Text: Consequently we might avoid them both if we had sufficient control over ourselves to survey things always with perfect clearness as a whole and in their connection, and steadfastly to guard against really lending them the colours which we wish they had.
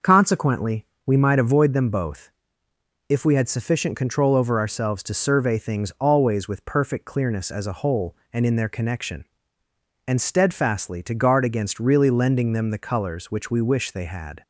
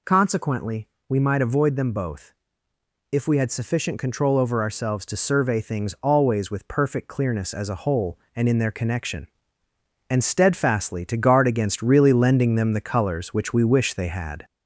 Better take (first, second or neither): first